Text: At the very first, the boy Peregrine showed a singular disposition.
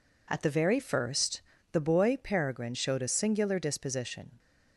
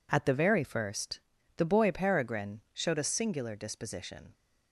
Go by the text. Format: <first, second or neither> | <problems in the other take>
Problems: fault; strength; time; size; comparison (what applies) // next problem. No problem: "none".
neither | none